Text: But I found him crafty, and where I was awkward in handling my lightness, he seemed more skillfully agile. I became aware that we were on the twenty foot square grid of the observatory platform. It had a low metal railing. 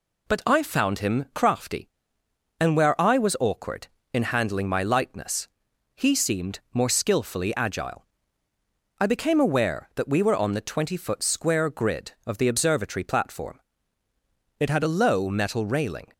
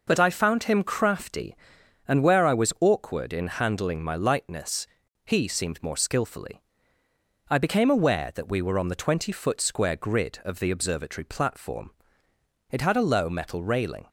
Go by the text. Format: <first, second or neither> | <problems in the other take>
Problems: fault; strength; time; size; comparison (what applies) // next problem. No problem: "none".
first | skips "agile"; at 7.0 s